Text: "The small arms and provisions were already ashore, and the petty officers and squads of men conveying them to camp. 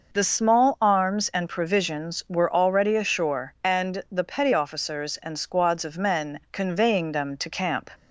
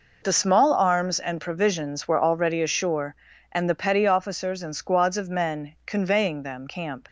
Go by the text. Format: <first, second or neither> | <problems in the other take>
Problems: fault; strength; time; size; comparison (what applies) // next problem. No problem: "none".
first | skips "to"; at 6.6 s